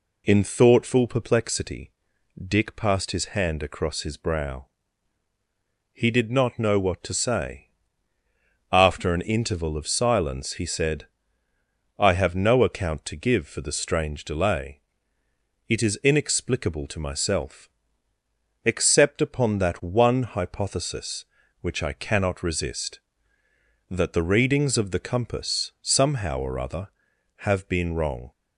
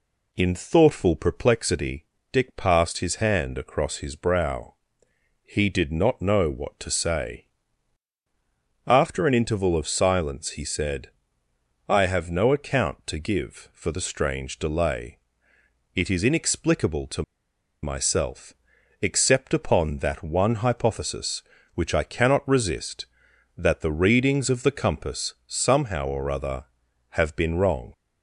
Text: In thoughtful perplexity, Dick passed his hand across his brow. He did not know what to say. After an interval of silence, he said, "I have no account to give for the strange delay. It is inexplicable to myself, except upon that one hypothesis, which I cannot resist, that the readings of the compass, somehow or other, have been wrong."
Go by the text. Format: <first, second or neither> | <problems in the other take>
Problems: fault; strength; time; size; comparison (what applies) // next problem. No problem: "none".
first | pauses between "to" and "myself"; noticeable; at 17.2 s; 0.61 s long